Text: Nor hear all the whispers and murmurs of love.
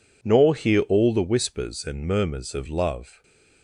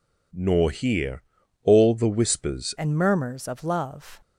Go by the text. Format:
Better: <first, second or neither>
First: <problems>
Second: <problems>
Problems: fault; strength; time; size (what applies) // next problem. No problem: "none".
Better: first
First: none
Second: pauses between "hear" and "all"; at 1.2 s; 0.40 s long // changes voice at "and"; from 2.7 s on; 1.5 s long